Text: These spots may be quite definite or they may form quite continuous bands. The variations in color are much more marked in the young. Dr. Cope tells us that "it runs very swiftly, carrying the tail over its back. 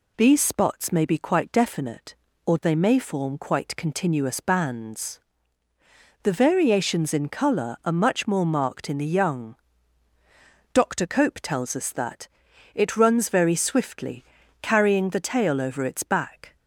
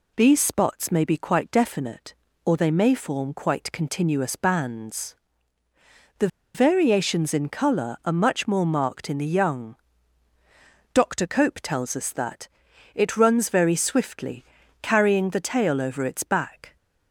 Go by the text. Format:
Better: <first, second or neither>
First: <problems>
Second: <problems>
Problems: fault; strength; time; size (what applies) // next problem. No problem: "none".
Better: first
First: pauses between "that" and "it"; noticeable; at 12.2 s; 0.48 s long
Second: pauses between "The" and "variations"; slight; at 6.2 s; 0.27 s long // pauses between "that" and "it"; noticeable; at 12.4 s; 0.48 s long